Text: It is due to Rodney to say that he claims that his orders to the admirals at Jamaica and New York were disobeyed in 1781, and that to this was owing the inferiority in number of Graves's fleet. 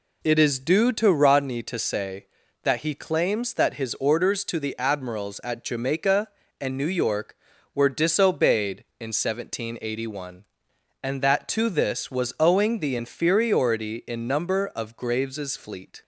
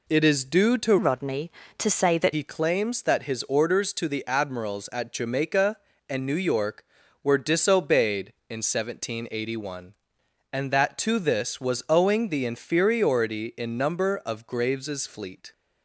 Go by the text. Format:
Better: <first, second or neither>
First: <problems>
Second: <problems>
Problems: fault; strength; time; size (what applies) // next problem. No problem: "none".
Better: first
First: none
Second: changes voice from "Rodney" to "that"; from 0.9 to 2.3 s; 1.4 s long